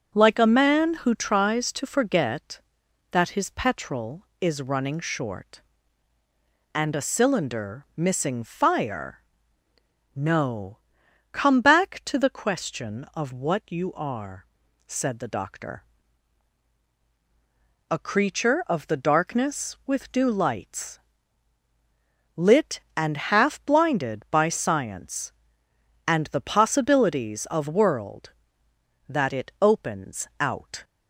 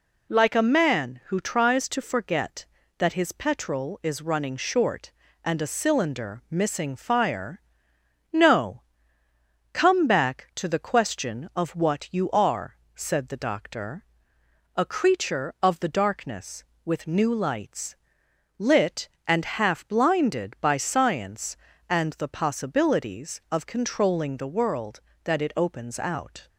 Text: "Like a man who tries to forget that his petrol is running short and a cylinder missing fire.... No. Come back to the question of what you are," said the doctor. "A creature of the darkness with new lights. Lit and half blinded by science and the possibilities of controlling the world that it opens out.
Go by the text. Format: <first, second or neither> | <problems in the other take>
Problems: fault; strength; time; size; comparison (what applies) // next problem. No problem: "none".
second | starts louder than the rest; until 1.2 s; 6.5 dB // pauses between "and" and "half"; slight; at 23.1 s; 0.16 s long // skips "controlling the"; at 27.6 s